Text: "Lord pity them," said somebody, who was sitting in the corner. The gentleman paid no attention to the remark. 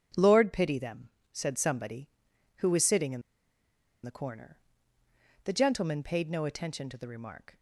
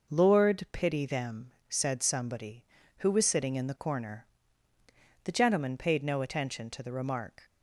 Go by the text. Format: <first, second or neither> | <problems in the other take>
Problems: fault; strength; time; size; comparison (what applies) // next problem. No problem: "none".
second | starts louder than the rest; strong; until 1.3 s; 7.5 dB // pauses between "in" and "the"; noticeable; at 3.2 s; 0.83 s long